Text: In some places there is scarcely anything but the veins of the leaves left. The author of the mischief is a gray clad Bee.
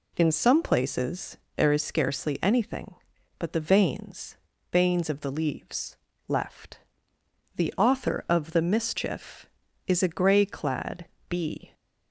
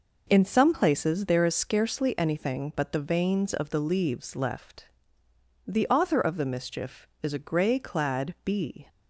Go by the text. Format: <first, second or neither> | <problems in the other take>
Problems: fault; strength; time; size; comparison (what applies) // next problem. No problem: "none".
second | pauses between "places" and "there"; slight; at 1.3 s; 0.18 s long // says "veins" twice; at 4.7 s // pauses between "leaves" and "left"; slight; at 5.9 s; 0.32 s long // pauses between "clad" and "Bee"; slight; at 11.0 s; 0.24 s long